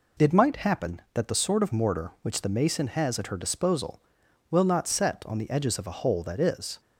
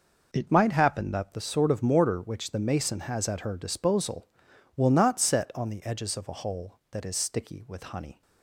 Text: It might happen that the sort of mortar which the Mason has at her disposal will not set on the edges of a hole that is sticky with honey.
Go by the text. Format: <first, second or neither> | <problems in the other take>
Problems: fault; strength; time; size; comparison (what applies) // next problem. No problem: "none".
second | stops before "sticky with honey"; at 6.7 s